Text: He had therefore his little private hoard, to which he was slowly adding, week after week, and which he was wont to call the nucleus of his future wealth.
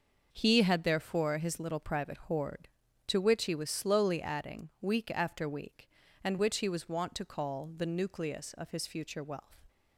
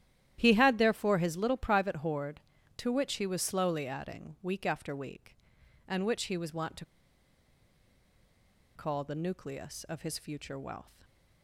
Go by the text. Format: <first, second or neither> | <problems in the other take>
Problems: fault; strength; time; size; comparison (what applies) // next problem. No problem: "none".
first | starts louder than the rest; strong; until 1.4 s; 12 dB; noticeable in the first // pauses between "to" and "call"; strong; at 6.8 s; 1.8 s long